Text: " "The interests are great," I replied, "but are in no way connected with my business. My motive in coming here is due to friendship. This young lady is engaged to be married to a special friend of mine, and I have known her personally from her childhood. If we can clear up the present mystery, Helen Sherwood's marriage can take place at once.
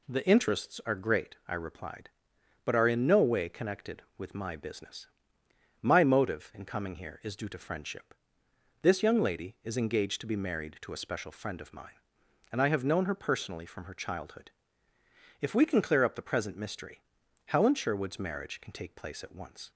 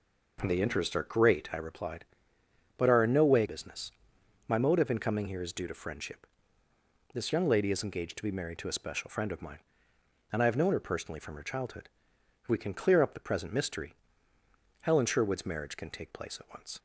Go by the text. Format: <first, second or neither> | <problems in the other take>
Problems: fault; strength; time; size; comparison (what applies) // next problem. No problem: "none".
first | skips "connected with my"; at 3.4 s